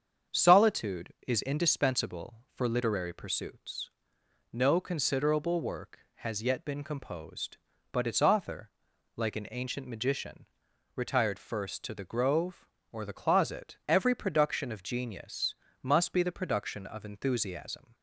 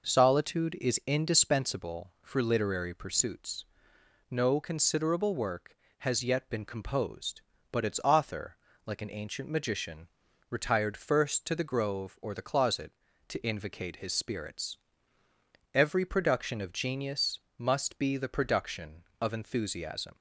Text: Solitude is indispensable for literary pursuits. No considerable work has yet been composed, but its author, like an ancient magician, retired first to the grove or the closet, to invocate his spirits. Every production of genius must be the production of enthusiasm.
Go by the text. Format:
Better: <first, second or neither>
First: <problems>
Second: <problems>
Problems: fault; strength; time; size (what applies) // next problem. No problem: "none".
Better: second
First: starts louder than the rest; strong; until 1.4 s; 7 dB // skips "to invocate his spirits"; at 13.8 s // pauses between "genius" and "must"; slight; at 15.5 s; 0.28 s long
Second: pauses between "genius" and "must"; slight; at 17.3 s; 0.18 s long